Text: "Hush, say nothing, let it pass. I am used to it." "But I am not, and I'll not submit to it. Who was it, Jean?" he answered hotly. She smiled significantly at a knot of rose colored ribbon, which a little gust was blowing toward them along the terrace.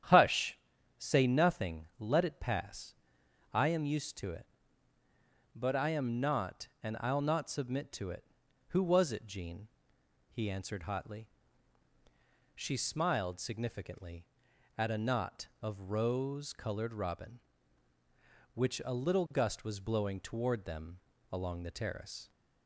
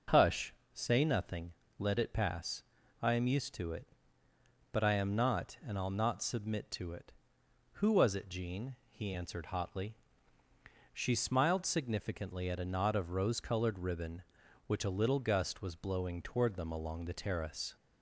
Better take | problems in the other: second | starts louder than the rest; strong; until 1.4 s; 10 dB // says "robin" for "ribbon"; at 16.9 s // pauses between "them" and "along"; slight; at 20.9 s; 0.30 s long

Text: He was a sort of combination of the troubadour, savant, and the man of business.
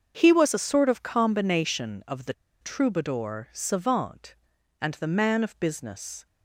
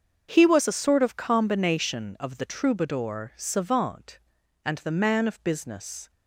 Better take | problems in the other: second | starts louder than the rest; until 1.1 s; 6.5 dB; also in the second // pauses between "the" and "troubadour"; slight; at 2.3 s; 0.29 s long

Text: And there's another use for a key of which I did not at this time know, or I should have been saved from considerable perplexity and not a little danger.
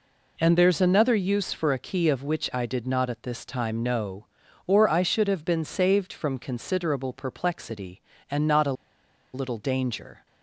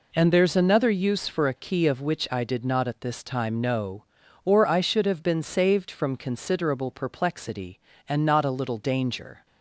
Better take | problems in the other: second | pauses between "a" and "little"; noticeable; at 8.7 s; 0.60 s long

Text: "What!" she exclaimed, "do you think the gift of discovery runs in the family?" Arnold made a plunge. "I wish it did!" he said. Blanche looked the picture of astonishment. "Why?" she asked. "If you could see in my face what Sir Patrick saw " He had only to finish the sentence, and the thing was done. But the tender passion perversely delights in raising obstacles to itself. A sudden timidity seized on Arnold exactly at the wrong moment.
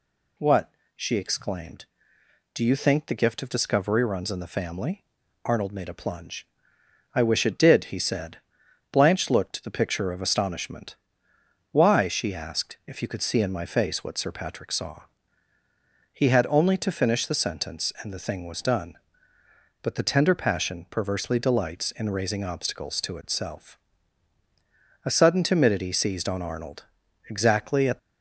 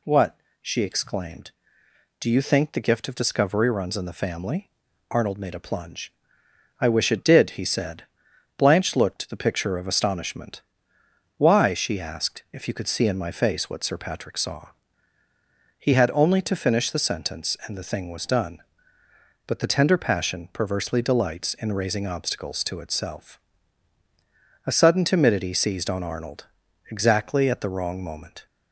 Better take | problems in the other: second | pauses between "Arnold" and "exactly"; noticeable; at 26.8 s; 0.46 s long; noticeable in the second // stops before "the wrong moment"; at 27.9 s

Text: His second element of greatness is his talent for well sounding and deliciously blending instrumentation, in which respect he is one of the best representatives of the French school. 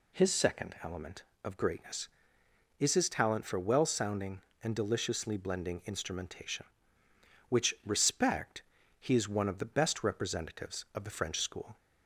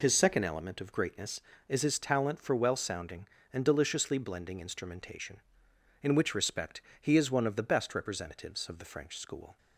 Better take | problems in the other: second | skips "in"; at 7.0 s // pauses between "respect" and "he"; at 8.6 s; 0.38 s long; slight in the second

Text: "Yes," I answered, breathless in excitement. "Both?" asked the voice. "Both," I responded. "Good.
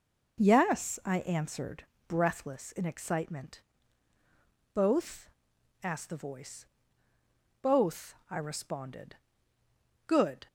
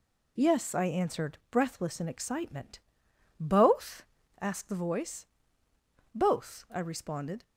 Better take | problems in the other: first | stops before "Good"; at 7.4 s

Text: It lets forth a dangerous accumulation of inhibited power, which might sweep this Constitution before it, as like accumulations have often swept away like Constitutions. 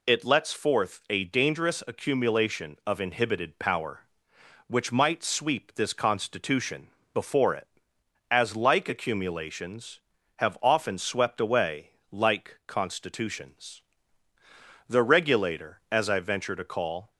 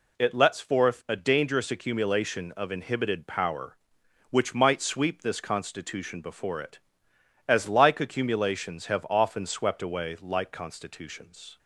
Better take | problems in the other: second | pauses between "Constitution" and "before"; slight; at 6.8 s; 0.26 s long // pauses between "away" and "like"; slight; at 11.9 s; 0.20 s long // goes on to say "The regulator as I venture to call"; strong; from 14.8 s on; 2.2 s long

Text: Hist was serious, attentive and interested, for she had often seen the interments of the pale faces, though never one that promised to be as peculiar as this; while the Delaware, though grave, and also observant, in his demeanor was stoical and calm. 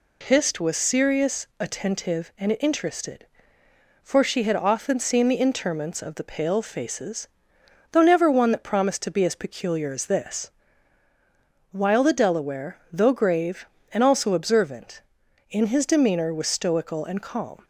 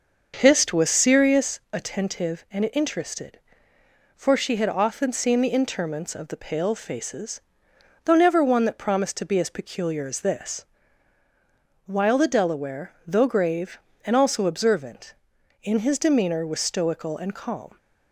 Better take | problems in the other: first | starts louder than the rest; until 1.6 s; 6 dB

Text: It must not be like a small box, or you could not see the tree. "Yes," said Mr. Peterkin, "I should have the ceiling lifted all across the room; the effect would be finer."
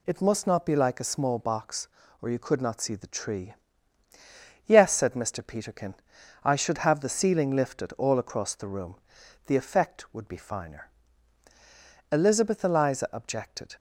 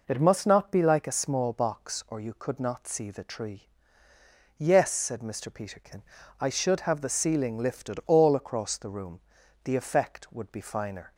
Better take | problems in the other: second | goes on to say "Elizabeth Eliza objected"; from 12.1 s on; 1.6 s long

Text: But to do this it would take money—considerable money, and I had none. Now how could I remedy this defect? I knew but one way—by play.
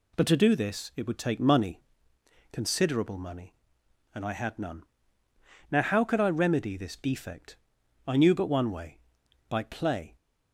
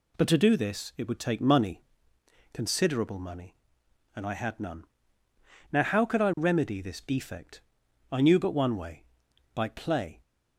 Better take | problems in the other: neither | none

